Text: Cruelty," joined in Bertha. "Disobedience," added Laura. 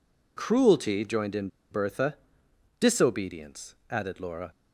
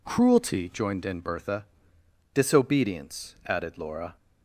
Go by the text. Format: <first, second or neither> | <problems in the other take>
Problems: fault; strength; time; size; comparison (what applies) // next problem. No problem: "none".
second | pauses between "in" and "Bertha"; slight; at 1.4 s; 0.23 s long